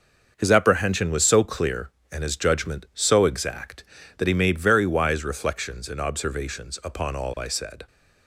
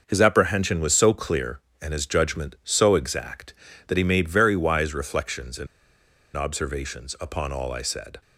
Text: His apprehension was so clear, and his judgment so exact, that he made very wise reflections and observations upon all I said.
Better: first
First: starts louder than the rest; noticeable; until 1.3 s; 6 dB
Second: starts louder than the rest; noticeable; until 1.0 s; 6 dB // pauses between "and" and "observations"; noticeable; at 5.6 s; 0.69 s long

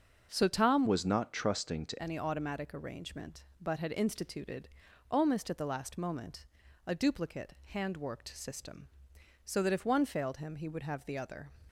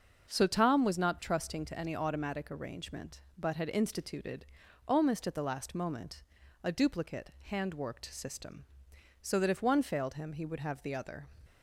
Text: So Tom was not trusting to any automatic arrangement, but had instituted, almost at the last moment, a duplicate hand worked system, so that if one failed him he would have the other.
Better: second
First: starts louder than the rest; until 1.3 s; 6.5 dB // changes voice from "was" to "to"; from 0.8 to 2.0 s; 1.2 s long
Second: starts louder than the rest; until 1.3 s; 6.5 dB

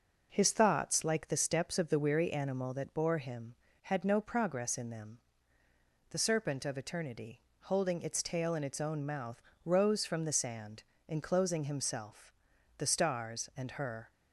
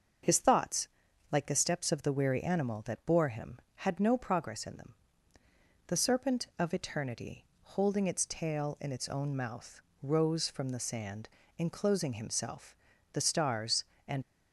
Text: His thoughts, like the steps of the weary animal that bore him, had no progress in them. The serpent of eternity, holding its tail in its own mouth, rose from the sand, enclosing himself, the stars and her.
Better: first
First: none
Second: starts louder than the rest; until 1.6 s; 6.5 dB // stops before "her"; at 14.2 s

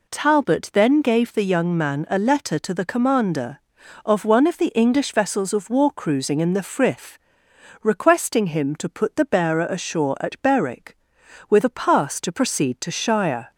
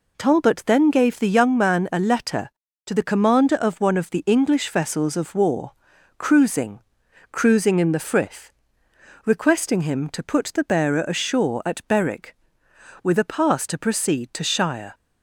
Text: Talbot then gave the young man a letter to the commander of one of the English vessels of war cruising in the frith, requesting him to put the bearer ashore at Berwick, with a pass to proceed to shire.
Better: first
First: none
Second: pauses between "war" and "cruising"; noticeable; at 5.7 s; 0.46 s long // says "cruising" twice; at 7.3 s

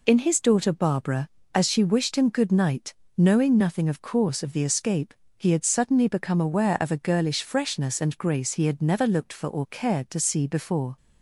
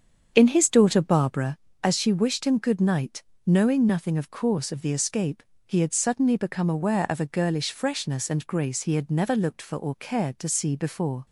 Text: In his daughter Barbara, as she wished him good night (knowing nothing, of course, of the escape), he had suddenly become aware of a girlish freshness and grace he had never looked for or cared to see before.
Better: first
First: none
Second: starts louder than the rest; strong; until 1.5 s; 7.5 dB

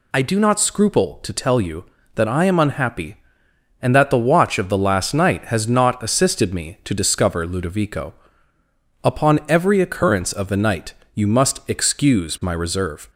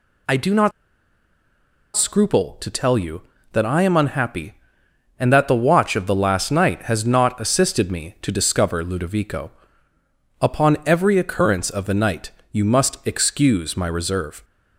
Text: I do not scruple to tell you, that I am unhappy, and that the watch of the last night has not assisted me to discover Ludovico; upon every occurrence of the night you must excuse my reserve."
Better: first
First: pauses between "night" and "you"; slight; at 10.9 s; 0.20 s long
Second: pauses between "not" and "scruple"; strong; at 0.7 s; 1.2 s long // pauses between "night" and "you"; slight; at 12.3 s; 0.20 s long

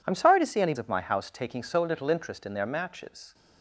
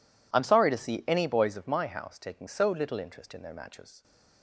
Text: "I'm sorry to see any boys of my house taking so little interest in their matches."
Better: second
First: skips "boys"; at 0.7 s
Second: none

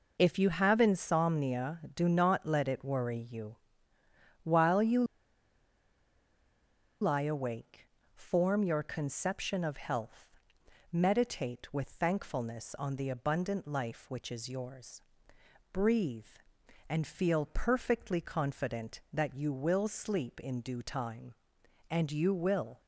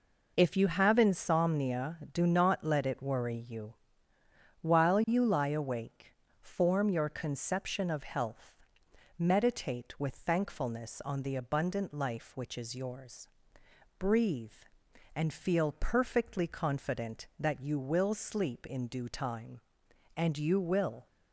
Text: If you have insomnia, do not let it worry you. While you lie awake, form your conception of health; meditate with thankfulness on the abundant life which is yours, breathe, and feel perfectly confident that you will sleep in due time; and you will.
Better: second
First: pauses between "you" and "lie"; strong; at 5.0 s; 1.9 s long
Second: none

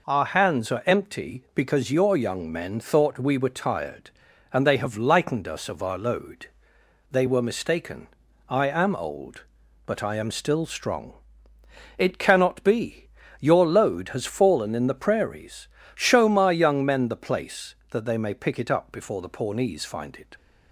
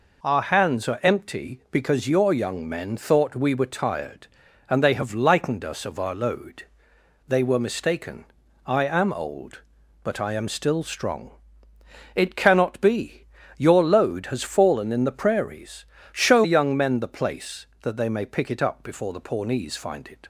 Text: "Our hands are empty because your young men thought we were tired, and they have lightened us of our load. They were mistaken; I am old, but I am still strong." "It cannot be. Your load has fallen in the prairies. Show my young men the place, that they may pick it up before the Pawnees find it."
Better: first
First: none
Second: skips "my"; at 16.4 s

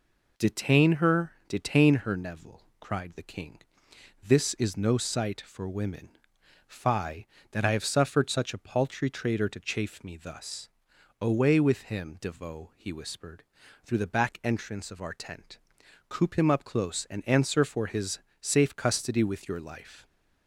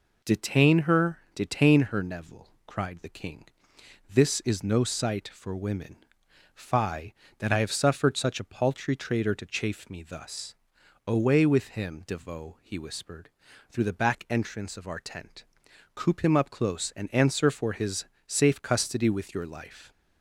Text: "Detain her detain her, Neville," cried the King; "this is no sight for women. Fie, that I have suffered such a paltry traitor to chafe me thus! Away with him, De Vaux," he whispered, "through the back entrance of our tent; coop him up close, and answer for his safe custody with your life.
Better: neither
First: pauses between "her" and "detain"; slight; at 1.3 s; 0.16 s long // pauses between "his" and "safe"; slight; at 18.1 s; 0.22 s long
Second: pauses between "her" and "detain"; slight; at 1.1 s; 0.16 s long // pauses between "his" and "safe"; slight; at 18.0 s; 0.22 s long

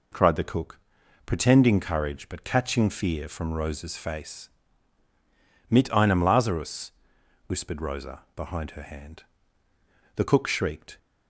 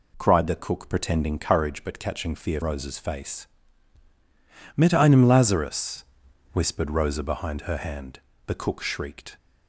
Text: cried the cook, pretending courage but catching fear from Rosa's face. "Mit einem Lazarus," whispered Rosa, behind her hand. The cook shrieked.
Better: first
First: none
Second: skips "from"; at 2.6 s

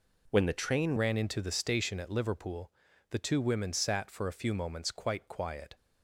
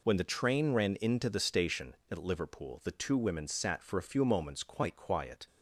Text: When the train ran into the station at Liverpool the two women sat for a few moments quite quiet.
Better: second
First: changes voice at "ran"; from 0.9 s on; 4.8 s long // pauses between "Liverpool" and "the"; at 2.7 s; 0.38 s long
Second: none

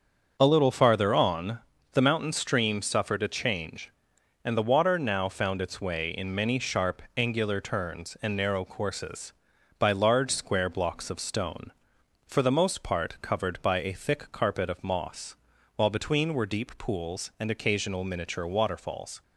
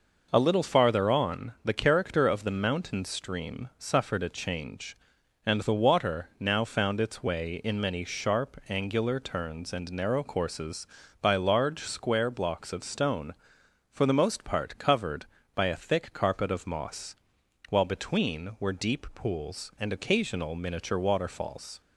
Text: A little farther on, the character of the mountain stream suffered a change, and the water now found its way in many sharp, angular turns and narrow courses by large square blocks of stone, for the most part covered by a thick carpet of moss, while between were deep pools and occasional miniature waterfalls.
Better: second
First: starts louder than the rest; until 1.4 s; 7 dB // skips "the character of"; at 1.7 s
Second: none

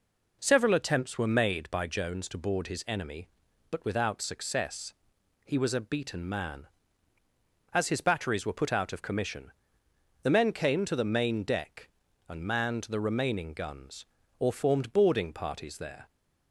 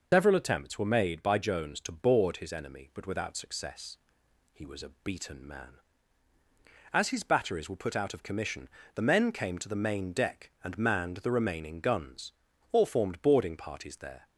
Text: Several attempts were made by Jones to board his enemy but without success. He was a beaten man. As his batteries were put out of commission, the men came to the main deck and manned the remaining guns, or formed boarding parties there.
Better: first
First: none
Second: loses the start of "Several"; at 0.1 s; 125 ms

